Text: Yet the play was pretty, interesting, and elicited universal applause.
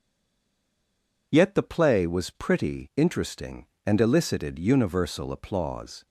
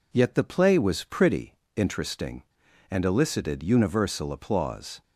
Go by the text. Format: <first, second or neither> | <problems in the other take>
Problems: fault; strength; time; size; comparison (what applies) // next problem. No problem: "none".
second | stays silent before the first word; noticeable; until 1.3 s; 1.3 s long